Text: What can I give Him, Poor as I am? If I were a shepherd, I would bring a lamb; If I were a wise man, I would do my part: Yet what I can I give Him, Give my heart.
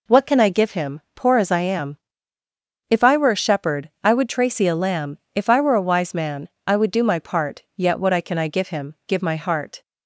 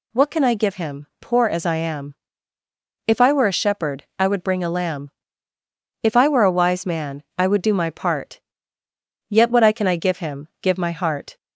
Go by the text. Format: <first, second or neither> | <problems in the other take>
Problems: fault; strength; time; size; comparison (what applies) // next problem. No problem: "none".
second | says "tracy" for "bring"; at 4.2 s